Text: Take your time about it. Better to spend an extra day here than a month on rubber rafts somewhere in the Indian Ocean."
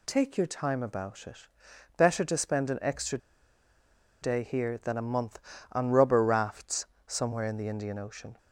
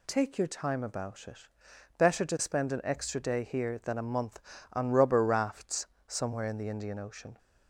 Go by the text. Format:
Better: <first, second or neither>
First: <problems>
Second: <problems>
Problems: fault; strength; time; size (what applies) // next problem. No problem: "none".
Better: second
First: pauses between "extra" and "day"; at 3.1 s; 1.0 s long // pauses between "rafts" and "somewhere"; slight; at 6.8 s; 0.22 s long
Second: pauses between "rafts" and "somewhere"; slight; at 5.8 s; 0.22 s long